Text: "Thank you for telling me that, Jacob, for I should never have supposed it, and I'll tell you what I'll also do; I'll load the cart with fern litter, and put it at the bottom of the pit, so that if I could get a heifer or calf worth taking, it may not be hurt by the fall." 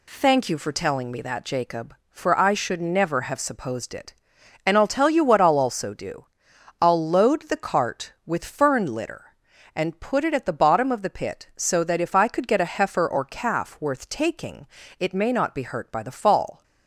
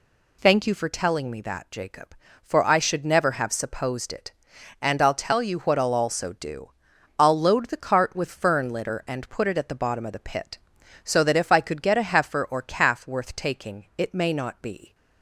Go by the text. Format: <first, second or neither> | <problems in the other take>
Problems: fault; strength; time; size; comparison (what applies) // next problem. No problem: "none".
first | stops before "hurt by the fall"; at 14.9 s